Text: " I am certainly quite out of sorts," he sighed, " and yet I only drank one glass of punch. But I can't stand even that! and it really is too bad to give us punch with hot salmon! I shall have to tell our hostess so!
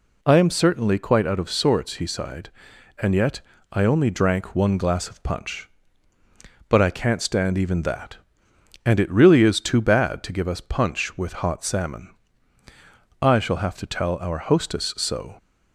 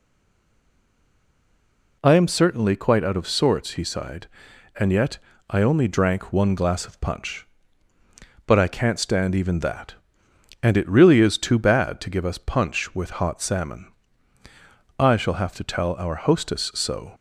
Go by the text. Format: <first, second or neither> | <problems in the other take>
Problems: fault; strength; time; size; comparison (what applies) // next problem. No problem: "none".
first | stays silent before the first word; noticeable; until 2.0 s; 2.0 s long // pauses between "yet" and "I"; slight; at 5.1 s; 0.30 s long; slight in the first